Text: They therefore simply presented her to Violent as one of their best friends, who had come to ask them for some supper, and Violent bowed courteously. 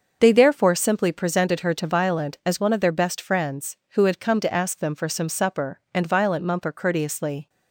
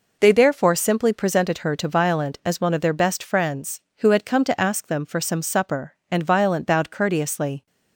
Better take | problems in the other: second | starts louder than the rest; until 1.2 s; 6.5 dB // says "mumper" for "bowed"; at 6.4 s

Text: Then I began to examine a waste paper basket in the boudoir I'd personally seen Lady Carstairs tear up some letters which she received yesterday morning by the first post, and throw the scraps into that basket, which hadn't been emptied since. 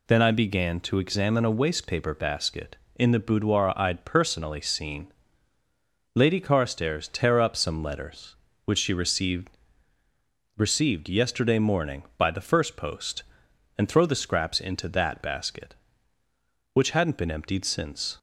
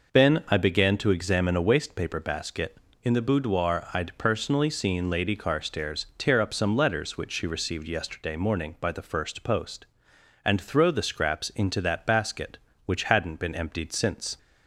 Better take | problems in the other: second | pauses between "seen" and "Lady"; at 5.0 s; 1.0 s long // says "received" twice; at 10.5 s

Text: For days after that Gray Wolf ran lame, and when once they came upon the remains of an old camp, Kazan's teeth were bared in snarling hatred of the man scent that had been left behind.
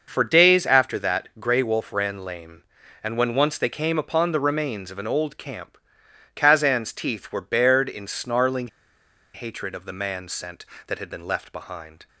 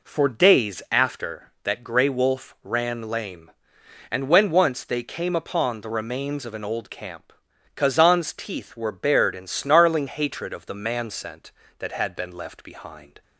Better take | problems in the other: second | starts louder than the rest; noticeable; until 1.1 s; 6 dB // pauses between "snarling" and "hatred"; noticeable; at 8.6 s; 0.65 s long

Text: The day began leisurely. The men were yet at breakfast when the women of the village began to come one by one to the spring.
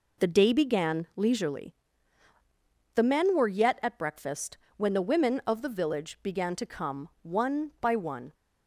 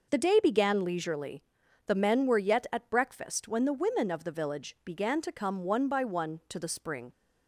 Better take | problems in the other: second | pauses between "breakfast" and "when"; slight; at 4.5 s; 0.18 s long // stops before "to the spring"; at 8.3 s

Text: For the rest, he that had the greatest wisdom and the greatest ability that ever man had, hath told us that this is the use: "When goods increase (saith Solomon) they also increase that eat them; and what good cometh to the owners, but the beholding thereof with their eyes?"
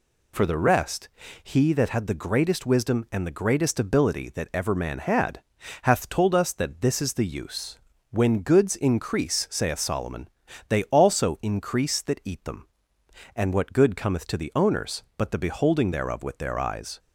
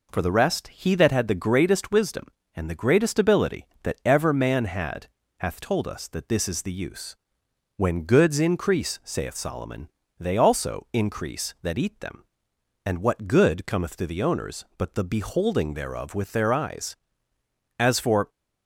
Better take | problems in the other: first | goes on to say "As for"; from 17.7 s on; 0.50 s long

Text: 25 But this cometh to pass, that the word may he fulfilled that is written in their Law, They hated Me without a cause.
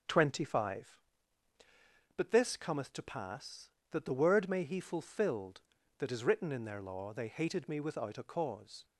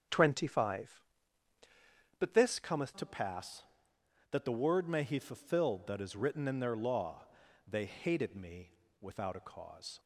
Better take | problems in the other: first | starts louder than the rest; until 2.3 s; 7 dB; noticeable in the first // changes voice at "to"; from 2.9 s on; 7.0 s long // pauses between "Me" and "without"; slight; at 8.7 s; 0.28 s long

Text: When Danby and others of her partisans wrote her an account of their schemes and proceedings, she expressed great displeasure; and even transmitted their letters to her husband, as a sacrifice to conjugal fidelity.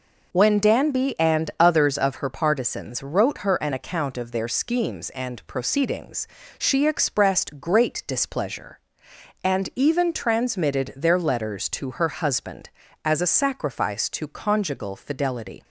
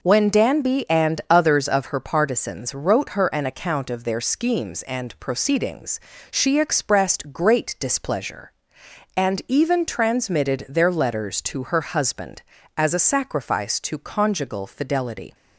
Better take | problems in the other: neither | none

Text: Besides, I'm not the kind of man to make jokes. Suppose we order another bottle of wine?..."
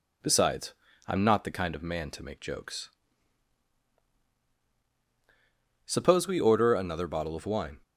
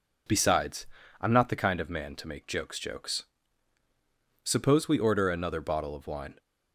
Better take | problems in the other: first | says "jokes" twice; at 2.7 s

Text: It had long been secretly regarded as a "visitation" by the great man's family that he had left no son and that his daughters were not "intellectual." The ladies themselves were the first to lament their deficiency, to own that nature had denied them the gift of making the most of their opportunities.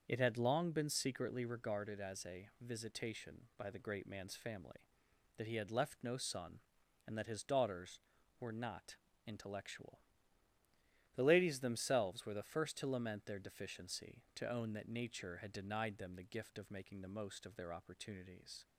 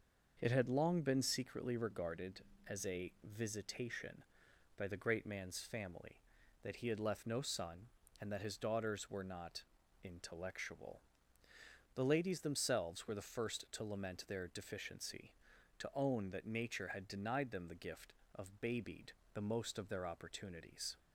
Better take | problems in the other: first | starts louder than the rest; until 1.4 s; 6 dB; also in the first // pauses between "not" and "intellectual"; at 9.6 s; 0.40 s long; slight in the first // says "babied" for "making"; at 18.6 s

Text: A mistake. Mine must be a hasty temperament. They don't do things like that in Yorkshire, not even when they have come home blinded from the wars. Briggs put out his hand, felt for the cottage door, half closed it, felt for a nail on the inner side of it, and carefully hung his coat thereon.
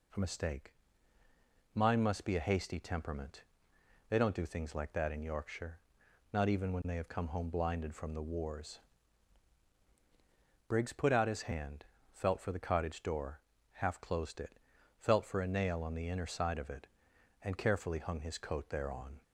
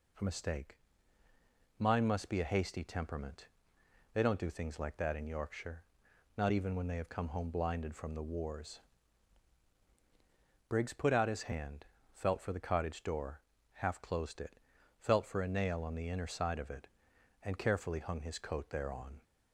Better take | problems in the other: neither | none

